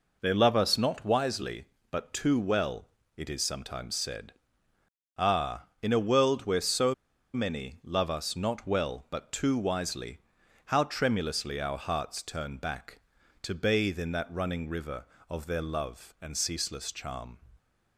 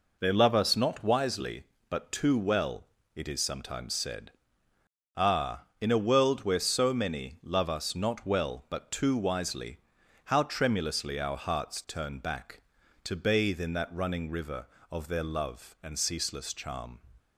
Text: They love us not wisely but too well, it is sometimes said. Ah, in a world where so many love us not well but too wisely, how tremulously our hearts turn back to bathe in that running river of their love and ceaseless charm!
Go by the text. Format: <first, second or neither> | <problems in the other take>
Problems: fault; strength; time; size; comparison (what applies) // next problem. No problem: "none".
second | pauses between "so" and "many"; at 6.9 s; 0.40 s long